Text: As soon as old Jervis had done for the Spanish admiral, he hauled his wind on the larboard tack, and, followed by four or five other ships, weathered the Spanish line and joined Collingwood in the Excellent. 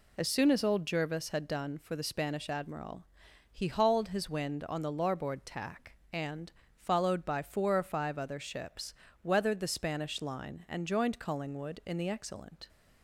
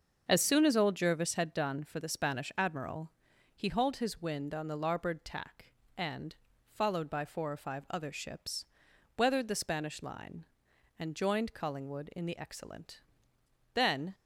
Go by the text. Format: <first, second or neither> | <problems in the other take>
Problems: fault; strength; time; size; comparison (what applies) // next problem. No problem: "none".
first | starts louder than the rest; until 1.2 s; 6.5 dB // goes on to say "Then"; slight; from 13.7 s on; 0.40 s long